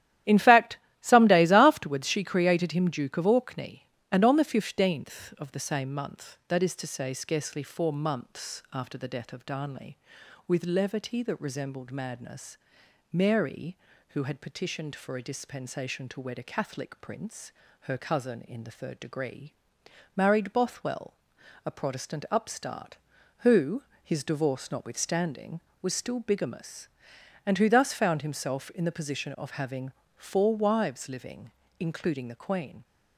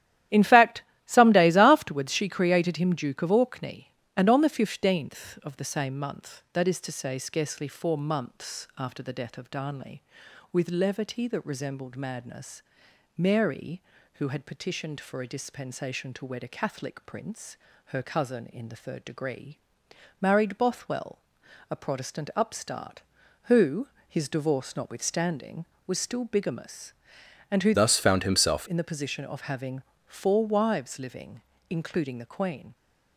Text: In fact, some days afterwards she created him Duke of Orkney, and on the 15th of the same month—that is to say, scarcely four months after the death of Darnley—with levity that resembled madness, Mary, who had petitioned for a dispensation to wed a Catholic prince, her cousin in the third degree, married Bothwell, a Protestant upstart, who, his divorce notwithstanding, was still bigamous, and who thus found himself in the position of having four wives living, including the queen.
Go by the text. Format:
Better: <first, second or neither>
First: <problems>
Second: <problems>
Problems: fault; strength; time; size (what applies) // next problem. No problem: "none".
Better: first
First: starts louder than the rest; strong; until 1.5 s; 12 dB // pauses between "having" and "four"; slight; at 29.9 s; 0.26 s long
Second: starts louder than the rest; strong; until 1.5 s; 12 dB // changes voice from "thus" to "himself"; from 27.7 to 28.6 s; 0.9 s long // pauses between "having" and "four"; slight; at 29.8 s; 0.26 s long